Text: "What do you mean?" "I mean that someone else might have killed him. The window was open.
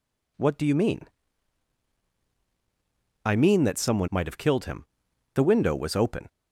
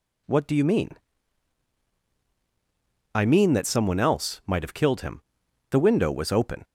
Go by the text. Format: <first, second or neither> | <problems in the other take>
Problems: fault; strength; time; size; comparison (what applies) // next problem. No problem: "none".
second | skips "else"; at 4.0 s